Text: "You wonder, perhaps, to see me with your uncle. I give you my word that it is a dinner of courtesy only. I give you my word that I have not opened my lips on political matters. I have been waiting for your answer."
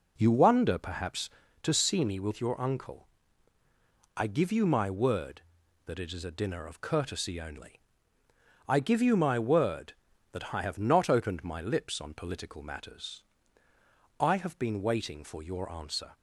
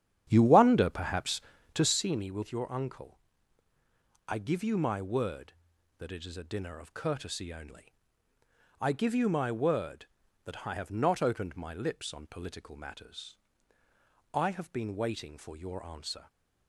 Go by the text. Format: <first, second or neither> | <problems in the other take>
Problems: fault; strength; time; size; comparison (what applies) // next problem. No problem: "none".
first | starts louder than the rest; strong; until 2.0 s; 9.5 dB